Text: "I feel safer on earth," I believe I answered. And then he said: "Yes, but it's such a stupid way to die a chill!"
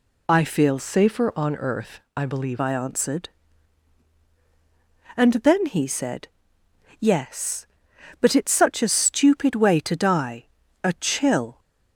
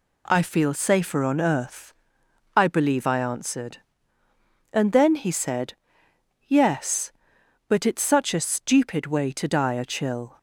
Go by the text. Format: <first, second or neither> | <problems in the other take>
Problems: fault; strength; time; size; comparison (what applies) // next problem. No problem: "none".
second | changes voice from "safer" to "believe"; from 0.7 to 2.5 s; 1.8 s long // pauses between "die" and "a"; at 10.4 s; 0.38 s long